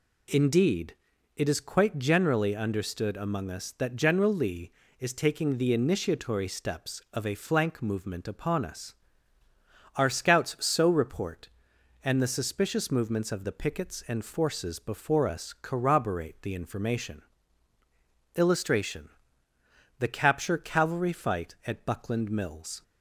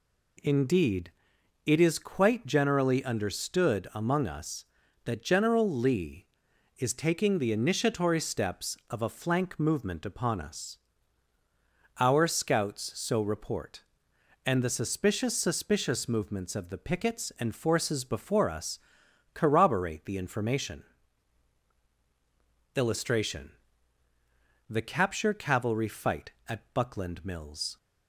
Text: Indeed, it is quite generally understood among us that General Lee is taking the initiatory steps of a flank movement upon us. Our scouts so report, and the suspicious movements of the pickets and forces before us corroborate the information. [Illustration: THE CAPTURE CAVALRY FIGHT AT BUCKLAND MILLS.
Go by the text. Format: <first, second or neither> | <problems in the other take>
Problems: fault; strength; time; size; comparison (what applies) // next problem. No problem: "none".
first | says "suspicious" twice; at 15.3 s // pauses between "us" and "corroborate"; noticeable; at 18.7 s; 0.56 s long